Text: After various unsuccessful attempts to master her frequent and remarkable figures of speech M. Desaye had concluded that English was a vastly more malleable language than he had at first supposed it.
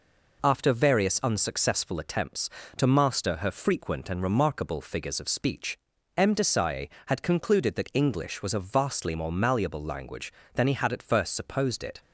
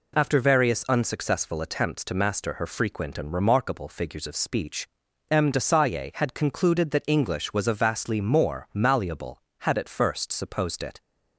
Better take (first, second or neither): first